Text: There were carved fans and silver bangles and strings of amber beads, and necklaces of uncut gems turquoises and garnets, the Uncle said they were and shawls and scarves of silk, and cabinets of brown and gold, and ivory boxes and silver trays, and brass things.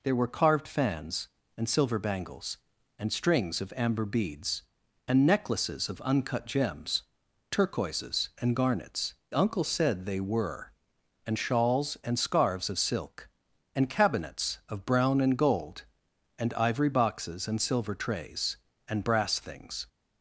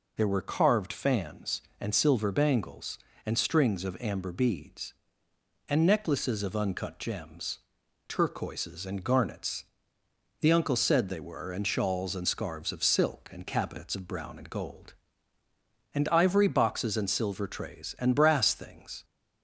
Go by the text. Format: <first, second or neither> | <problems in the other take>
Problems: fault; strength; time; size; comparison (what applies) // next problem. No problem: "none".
second | pauses between "gems" and "turquoises"; noticeable; at 7.0 s; 0.48 s long; noticeable in the second // skips "the"; at 9.2 s